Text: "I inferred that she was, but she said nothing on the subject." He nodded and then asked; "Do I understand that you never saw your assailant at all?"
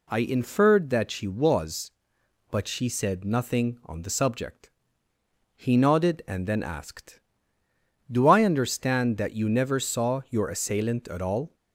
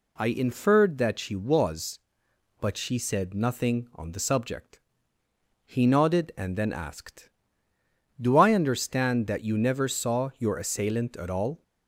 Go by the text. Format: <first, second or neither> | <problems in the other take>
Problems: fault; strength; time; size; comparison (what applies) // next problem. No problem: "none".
neither | none